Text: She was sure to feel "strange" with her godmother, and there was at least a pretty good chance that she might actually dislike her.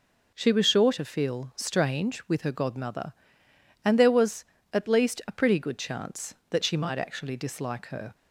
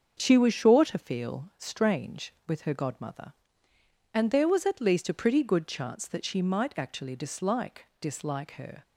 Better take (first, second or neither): first